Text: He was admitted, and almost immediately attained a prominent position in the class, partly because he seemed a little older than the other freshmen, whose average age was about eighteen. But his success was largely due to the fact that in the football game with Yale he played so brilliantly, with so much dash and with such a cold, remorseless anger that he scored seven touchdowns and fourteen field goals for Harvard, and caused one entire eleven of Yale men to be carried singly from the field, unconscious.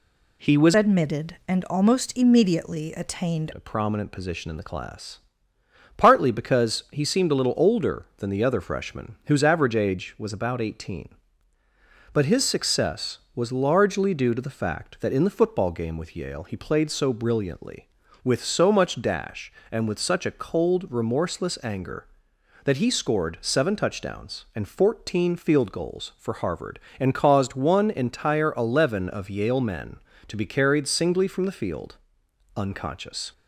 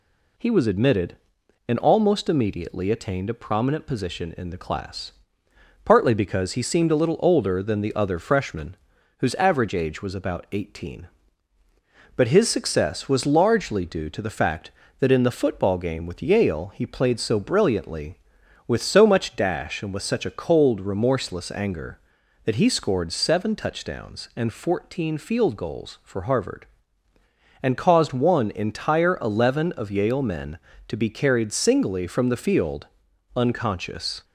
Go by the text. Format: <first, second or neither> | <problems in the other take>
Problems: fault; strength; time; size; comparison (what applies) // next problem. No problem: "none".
second | changes voice from "admitted" to "attained"; from 0.7 to 3.5 s; 2.8 s long